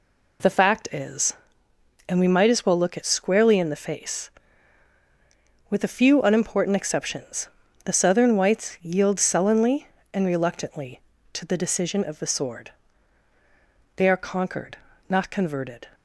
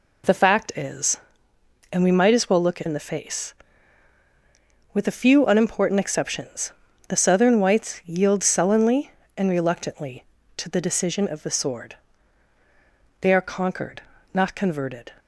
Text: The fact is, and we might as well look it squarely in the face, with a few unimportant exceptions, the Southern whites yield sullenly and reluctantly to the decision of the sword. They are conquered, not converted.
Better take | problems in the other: first | skips "squarely"; at 2.8 s

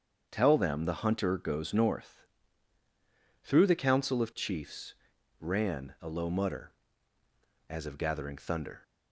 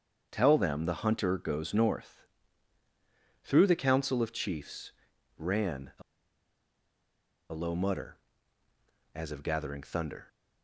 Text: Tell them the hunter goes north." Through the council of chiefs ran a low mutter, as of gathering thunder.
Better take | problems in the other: first | starts louder than the rest; strong; until 1.3 s; 7.5 dB; strong in the first // pauses between "chiefs" and "ran"; noticeable; at 4.9 s; 0.46 s long; noticeable in the first // pauses between "a" and "low"; strong; at 6.0 s; 1.5 s long

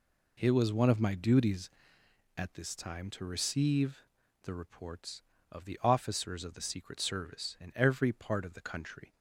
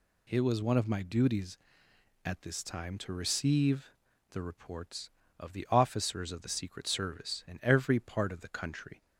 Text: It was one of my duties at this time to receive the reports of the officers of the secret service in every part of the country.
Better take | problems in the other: second | starts louder than the rest; slight; until 2.1 s; 3 dB // pauses between "receive" and "the"; at 3.9 s; 0.44 s long; also in the second

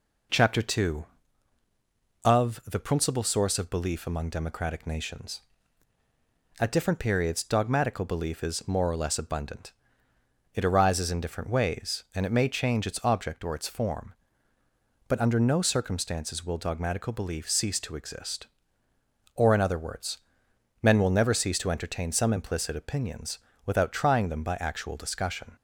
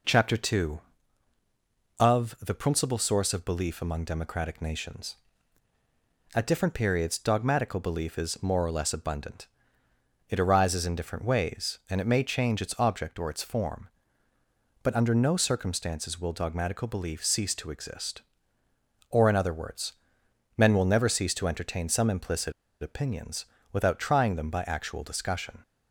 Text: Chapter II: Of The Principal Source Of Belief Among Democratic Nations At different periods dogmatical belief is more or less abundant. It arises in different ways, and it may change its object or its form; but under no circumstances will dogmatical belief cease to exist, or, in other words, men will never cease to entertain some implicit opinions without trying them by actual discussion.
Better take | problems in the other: first | pauses between "implicit" and "opinions"; slight; at 22.5 s; 0.29 s long // pauses between "opinions" and "without"; slight; at 23.4 s; 0.28 s long; slight in the first

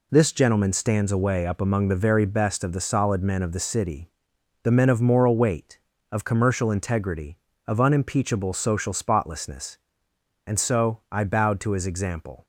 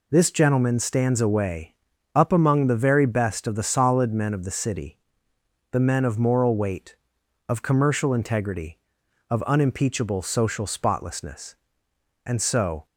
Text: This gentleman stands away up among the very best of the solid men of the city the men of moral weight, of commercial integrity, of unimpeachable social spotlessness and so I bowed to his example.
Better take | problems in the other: first | pauses between "away" and "up"; at 1.7 s; 0.40 s long // pauses between "city" and "the"; noticeable; at 4.9 s; 0.74 s long; noticeable in the first // stops before "I bowed to his example"; at 12.8 s

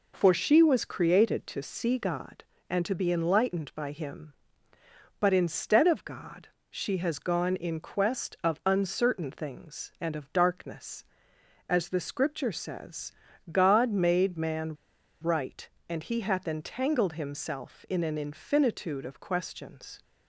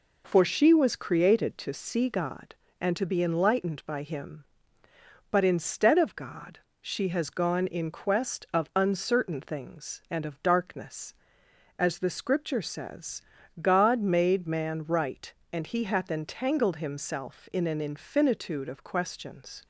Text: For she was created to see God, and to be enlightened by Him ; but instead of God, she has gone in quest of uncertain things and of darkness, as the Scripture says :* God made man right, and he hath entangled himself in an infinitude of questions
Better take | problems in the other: second | pauses between "man" and "right"; at 14.7 s; 0.45 s long

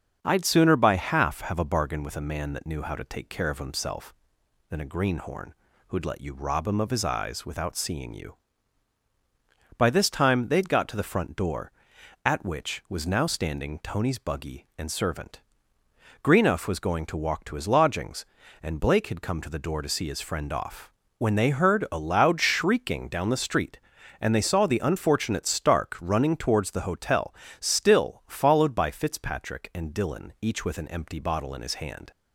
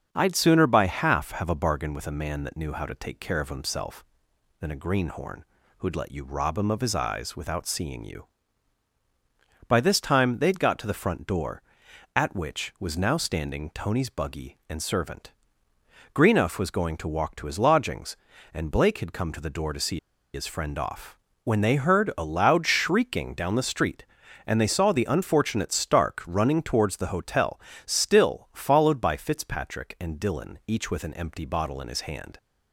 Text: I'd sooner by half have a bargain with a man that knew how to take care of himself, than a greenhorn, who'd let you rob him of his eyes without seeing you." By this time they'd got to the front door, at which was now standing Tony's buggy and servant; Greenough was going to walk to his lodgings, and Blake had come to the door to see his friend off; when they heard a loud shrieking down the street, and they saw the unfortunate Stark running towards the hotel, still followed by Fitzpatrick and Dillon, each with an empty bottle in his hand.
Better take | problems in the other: first | starts louder than the rest; until 1.1 s; 7 dB; also in the first // pauses between "see" and "his"; slight; at 19.9 s; 0.35 s long

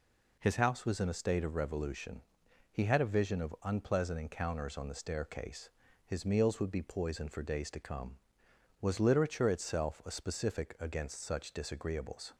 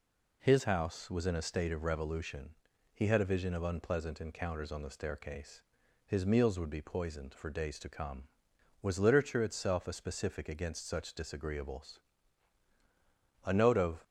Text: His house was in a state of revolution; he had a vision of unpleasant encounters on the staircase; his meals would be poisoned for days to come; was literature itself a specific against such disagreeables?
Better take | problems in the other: first | goes on to say "A note of"; from 13.4 s on; 0.58 s long

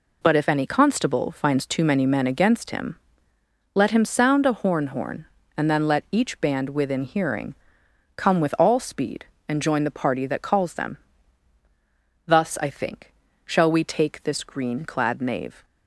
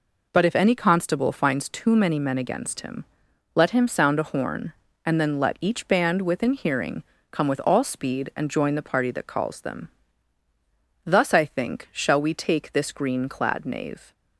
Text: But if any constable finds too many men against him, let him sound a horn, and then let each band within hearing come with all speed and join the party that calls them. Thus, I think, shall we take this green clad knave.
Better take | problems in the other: second | says "horn" twice; at 4.8 s // pauses between "hearing" and "come"; noticeable; at 7.5 s; 0.60 s long; slight in the second

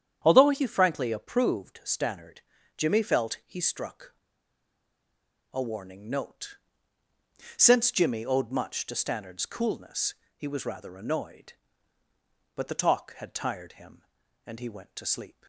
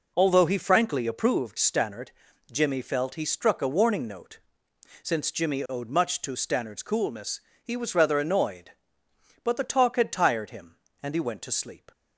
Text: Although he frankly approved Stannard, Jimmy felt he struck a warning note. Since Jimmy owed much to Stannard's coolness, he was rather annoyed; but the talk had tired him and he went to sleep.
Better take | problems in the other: second | starts louder than the rest; strong; until 1.2 s; 8.5 dB // pauses between "struck" and "a"; strong; at 4.1 s; 1.4 s long

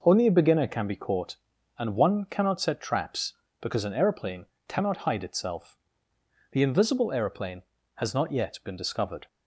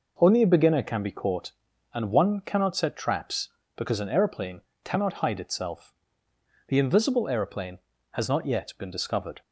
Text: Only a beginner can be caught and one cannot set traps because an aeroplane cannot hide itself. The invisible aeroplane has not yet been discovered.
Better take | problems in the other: neither | pauses between "aeroplane" and "cannot"; slight; the same in both

